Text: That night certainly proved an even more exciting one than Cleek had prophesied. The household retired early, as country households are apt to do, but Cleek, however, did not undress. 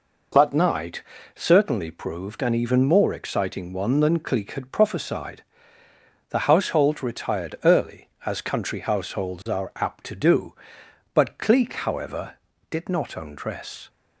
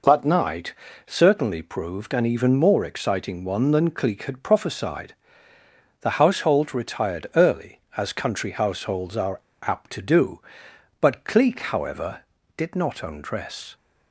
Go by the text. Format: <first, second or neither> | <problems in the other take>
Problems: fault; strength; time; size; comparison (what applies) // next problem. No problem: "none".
first | pauses between "night" and "certainly"; slight; at 0.7 s; 0.32 s long; slight in the first // pauses between "are" and "apt"; slight; at 9.3 s; 0.24 s long